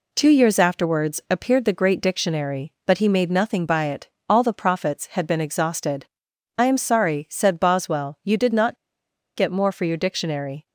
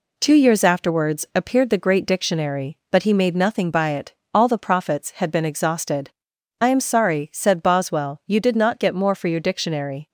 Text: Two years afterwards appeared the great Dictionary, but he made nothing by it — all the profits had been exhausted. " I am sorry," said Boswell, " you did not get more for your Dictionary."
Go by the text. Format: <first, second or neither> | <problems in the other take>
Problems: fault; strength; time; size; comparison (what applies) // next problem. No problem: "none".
second | pauses between "not" and "get"; noticeable; at 8.7 s; 0.60 s long